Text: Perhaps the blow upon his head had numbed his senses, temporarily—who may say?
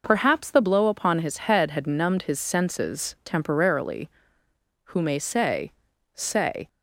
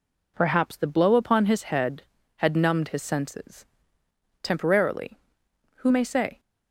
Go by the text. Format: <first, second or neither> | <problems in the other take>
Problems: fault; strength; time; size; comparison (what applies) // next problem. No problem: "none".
second | says "say" twice; at 6.1 s